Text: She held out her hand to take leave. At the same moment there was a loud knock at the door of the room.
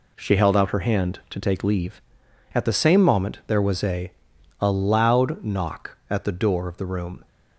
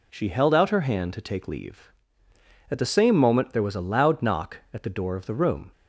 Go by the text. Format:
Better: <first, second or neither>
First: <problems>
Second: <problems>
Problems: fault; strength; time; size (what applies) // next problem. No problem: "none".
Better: second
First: says "a" twice; at 4.6 s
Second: none